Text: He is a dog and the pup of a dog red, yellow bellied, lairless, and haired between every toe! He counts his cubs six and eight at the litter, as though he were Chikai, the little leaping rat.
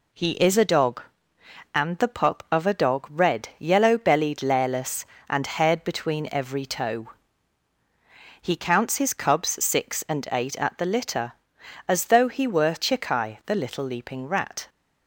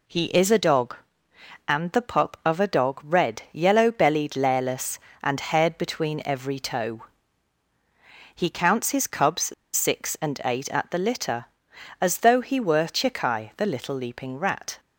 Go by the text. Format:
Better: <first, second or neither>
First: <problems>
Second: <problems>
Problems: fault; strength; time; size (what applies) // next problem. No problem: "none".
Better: first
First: none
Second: pauses between "cubs" and "six"; slight; at 9.5 s; 0.21 s long